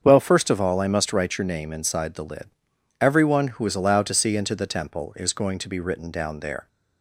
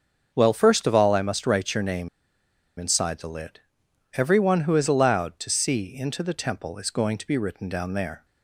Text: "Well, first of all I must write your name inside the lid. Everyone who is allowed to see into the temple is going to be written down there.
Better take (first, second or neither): first